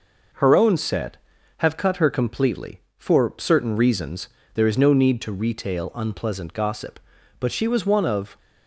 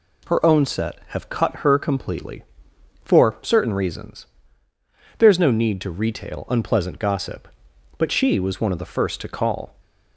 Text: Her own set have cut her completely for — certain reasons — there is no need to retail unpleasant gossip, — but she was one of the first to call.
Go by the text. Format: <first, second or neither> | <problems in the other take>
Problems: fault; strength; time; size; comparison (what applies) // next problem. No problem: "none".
second | stops before "the first to call"; at 8.3 s